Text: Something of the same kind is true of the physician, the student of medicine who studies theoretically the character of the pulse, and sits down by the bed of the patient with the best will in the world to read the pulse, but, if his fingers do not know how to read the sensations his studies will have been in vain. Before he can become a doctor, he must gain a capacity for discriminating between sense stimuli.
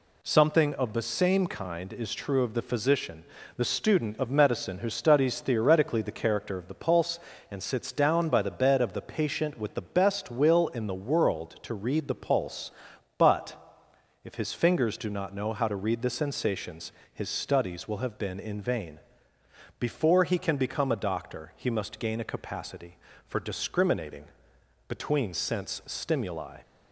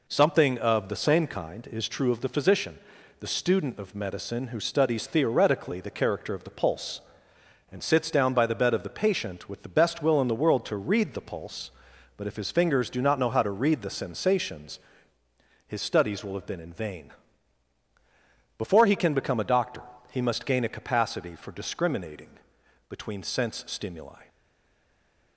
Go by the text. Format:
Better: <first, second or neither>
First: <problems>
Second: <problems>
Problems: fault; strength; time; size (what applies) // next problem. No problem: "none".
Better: first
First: pauses between "sensations" and "his"; slight; at 16.9 s; 0.20 s long // pauses between "discriminating" and "between"; noticeable; at 24.2 s; 0.62 s long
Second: pauses between "sensations" and "his"; noticeable; at 14.8 s; 0.88 s long // pauses between "discriminating" and "between"; noticeable; at 22.3 s; 0.58 s long // stays silent after the last word; from 24.2 s on; 1.1 s long